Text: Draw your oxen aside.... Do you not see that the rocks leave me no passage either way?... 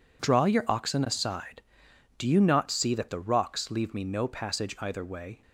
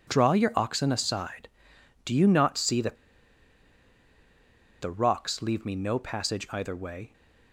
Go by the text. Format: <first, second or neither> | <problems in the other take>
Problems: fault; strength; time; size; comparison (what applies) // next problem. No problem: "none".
first | pauses between "that" and "the"; strong; at 2.9 s; 1.8 s long